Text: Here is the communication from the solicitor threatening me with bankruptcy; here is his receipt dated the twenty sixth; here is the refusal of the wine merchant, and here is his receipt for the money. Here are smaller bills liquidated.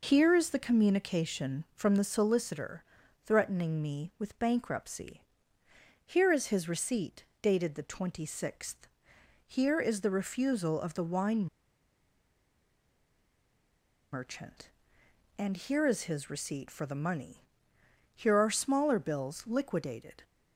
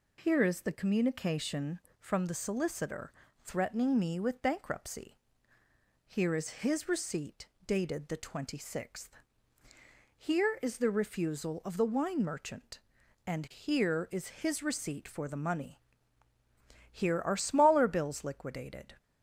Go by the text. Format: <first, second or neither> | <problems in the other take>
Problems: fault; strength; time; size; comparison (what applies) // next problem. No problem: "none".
second | pauses between "solicitor" and "threatening"; at 2.8 s; 0.40 s long; slight in the second // pauses between "receipt" and "dated"; slight; at 7.2 s; 0.16 s long; slight in the second // pauses between "wine" and "merchant"; strong; at 11.4 s; 2.6 s long